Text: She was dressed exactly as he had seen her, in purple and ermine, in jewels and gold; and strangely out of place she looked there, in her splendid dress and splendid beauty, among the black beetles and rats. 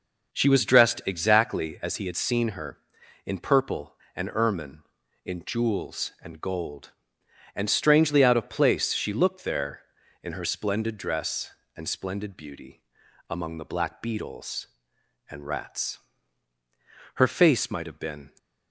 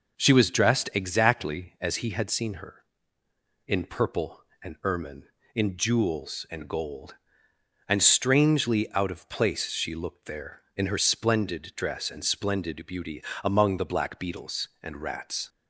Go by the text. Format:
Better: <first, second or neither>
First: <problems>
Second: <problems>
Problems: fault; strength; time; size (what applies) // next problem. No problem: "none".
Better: second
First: goes on to say "Her face might have been"; noticeable; from 17.1 s on; 1.1 s long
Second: none